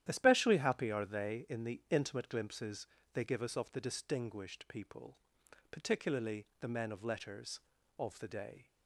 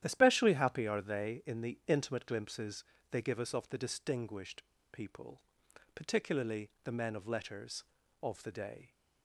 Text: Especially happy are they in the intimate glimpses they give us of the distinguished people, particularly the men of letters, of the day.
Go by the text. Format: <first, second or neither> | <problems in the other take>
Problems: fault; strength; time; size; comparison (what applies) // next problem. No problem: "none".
first | starts louder than the rest; strong; until 1.0 s; 11.5 dB; strong in the first // pauses between "glimpses" and "they"; slight; at 2.8 s; 0.28 s long; slight in the first // pauses between "distinguished" and "people"; slight; at 4.6 s; 0.28 s long